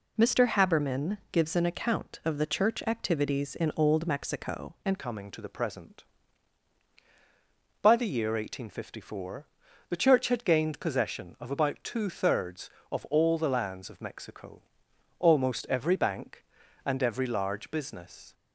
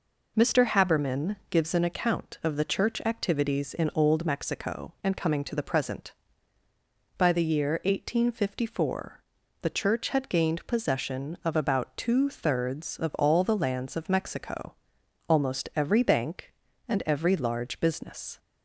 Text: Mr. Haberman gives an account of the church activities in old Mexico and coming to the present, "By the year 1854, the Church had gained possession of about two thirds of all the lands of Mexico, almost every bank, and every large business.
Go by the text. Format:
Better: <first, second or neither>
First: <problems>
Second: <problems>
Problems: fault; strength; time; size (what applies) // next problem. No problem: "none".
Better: second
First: changes voice at "coming"; from 4.9 s on; 13.4 s long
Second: none